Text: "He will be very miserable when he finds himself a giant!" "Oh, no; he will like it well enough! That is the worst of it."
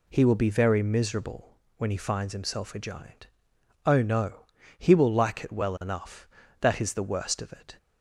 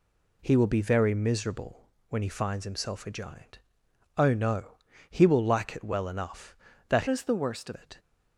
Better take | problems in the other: first | pauses between "miserable" and "when"; slight; at 1.8 s; 0.18 s long; slight in the first // changes voice from "is" to "of"; from 7.0 to 7.7 s; 0.7 s long

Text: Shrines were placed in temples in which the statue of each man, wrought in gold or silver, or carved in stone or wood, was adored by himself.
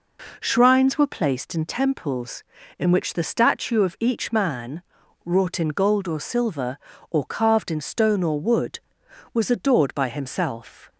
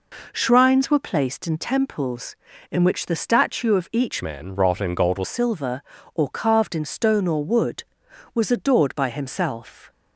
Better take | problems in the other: first | changes voice from "man" to "or"; from 4.2 to 5.2 s; 1.0 s long

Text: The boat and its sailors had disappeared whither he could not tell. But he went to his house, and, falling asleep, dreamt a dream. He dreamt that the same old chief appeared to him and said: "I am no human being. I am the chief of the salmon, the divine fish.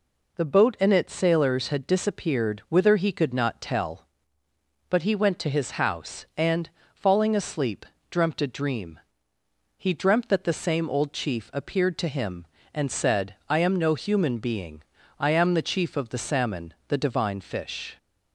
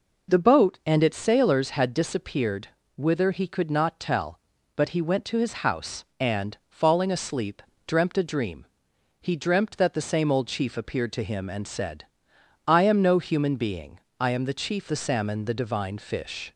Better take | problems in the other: first | pauses between "disappeared" and "whither"; slight; at 2.6 s; 0.28 s long // skips "of"; at 14.8 s

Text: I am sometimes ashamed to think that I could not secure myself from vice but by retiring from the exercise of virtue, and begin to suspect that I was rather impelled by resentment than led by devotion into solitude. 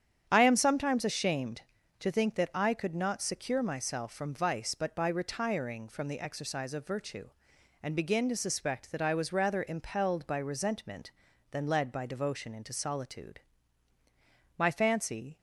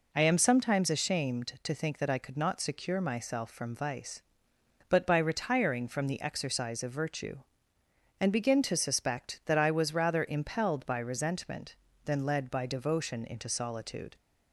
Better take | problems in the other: second | starts louder than the rest; strong; until 1.2 s; 8.5 dB // goes on to say "My fancy"; noticeable; from 14.5 s on; 0.80 s long

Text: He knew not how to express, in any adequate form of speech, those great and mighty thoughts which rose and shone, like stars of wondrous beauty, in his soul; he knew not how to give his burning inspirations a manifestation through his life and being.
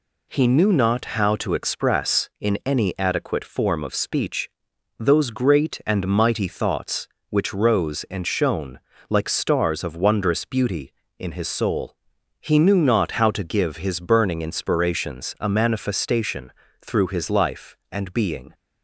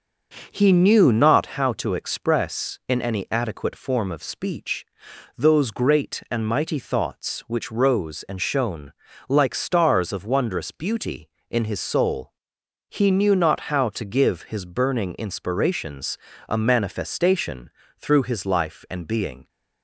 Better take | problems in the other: first | starts louder than the rest; noticeable; until 1.6 s; 6 dB // pauses between "inspirations" and "a"; slight; at 16.1 s; 0.32 s long // pauses between "manifestation" and "through"; slight; at 17.6 s; 0.30 s long; slight in the first

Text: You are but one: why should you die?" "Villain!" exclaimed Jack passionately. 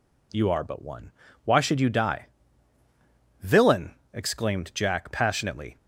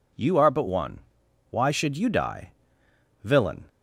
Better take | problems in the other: first | stops before "exclaimed Jack passionately"; at 3.6 s

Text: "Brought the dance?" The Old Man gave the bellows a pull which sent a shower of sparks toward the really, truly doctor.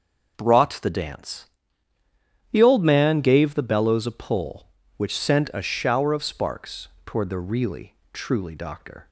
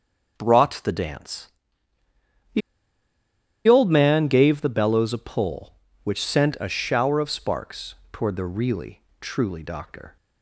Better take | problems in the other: first | starts louder than the rest; noticeable; until 1.4 s; 6 dB; noticeable in the first // pauses between "The" and "Old"; at 2.6 s; 1.0 s long // pauses between "sparks" and "toward"; slight; at 7.9 s; 0.18 s long; slight in the first

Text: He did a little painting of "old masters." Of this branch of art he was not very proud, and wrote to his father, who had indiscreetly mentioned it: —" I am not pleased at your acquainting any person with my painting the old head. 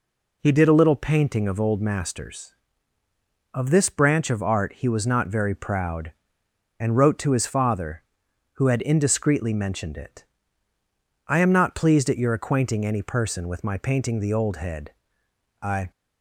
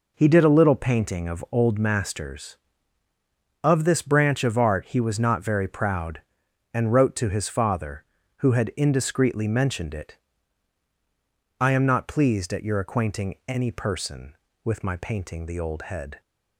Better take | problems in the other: second | goes on to say "I"; slight; from 15.6 s on; 0.30 s long

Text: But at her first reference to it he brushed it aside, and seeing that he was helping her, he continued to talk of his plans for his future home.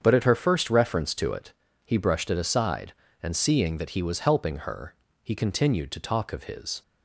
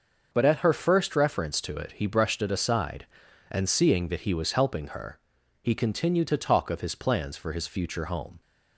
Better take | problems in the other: second | starts louder than the rest; strong; until 1.0 s; 7.5 dB; noticeable in the second // pauses between "it" and "he"; slight; at 1.5 s; 0.32 s long // stops before "plans for his future home"; at 6.8 s

